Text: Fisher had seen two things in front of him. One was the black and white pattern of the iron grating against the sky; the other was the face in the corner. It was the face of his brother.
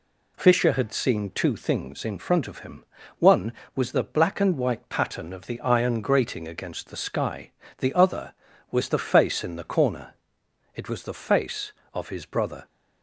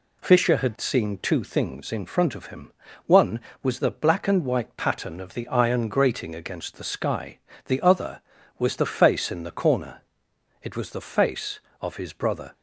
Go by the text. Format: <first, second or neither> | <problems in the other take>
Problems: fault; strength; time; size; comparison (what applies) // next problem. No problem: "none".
neither | none